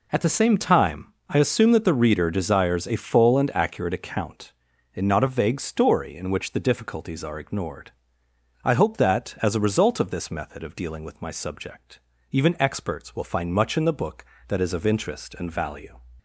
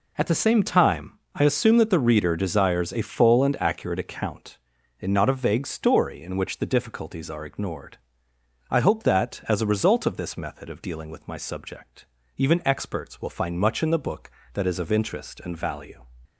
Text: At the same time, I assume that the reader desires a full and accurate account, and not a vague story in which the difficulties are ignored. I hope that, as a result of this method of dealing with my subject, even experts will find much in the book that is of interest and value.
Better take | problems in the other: neither | none

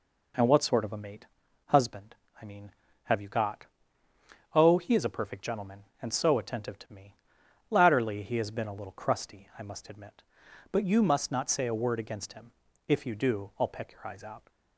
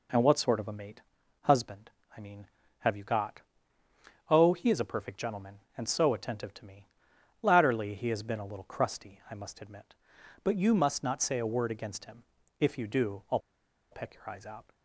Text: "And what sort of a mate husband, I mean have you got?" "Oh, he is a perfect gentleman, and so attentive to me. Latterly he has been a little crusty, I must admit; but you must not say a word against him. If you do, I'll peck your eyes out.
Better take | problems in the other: first | pauses between "mate" and "husband"; at 1.0 s; 0.42 s long; also in the first // pauses between "I'll" and "peck"; noticeable; at 13.3 s; 0.52 s long

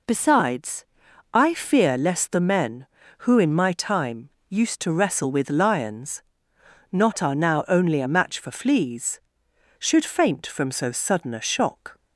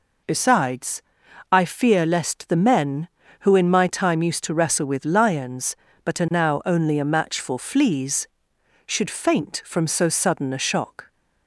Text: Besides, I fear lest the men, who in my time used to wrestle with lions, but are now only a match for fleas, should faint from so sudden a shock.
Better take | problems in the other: second | pauses between "time" and "used"; slight; at 4.2 s; 0.18 s long // says "not" for "but"; at 6.9 s

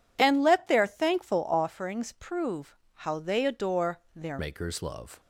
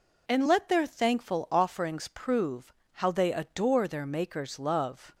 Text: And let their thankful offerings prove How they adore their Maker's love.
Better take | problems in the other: second | pauses between "prove" and "How"; slight; at 2.7 s; 0.16 s long; slight in the second // changes voice at "Maker's"; from 4.3 s on; 0.8 s long

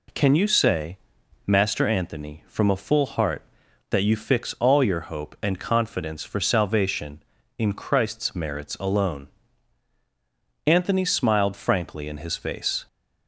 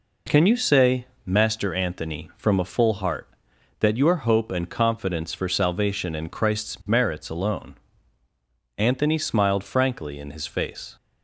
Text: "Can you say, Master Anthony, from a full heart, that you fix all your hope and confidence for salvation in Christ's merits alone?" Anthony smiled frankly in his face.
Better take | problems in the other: first | skips "you fix all"; at 3.9 s

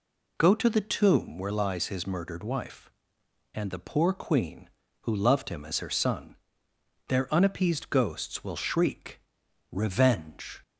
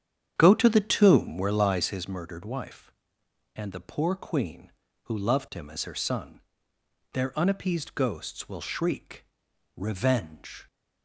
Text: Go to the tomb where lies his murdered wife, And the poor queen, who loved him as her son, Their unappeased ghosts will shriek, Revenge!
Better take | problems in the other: first | starts louder than the rest; strong; until 2.1 s; 9 dB

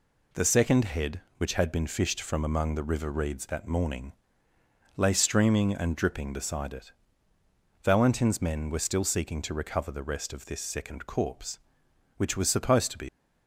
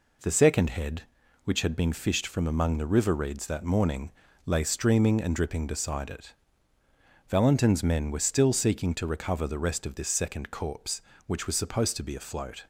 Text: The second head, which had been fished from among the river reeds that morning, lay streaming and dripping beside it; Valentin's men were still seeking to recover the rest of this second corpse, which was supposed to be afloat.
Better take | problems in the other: second | stops before "afloat"; at 13.0 s

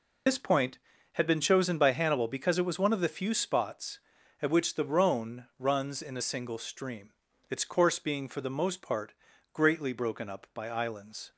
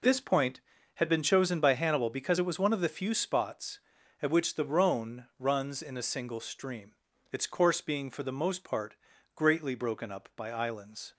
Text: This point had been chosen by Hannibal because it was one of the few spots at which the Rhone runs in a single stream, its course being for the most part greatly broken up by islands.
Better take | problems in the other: second | loses the start of "This"; at 0.2 s; 60 ms // pauses between "part" and "greatly"; at 9.1 s; 0.40 s long; also in the second

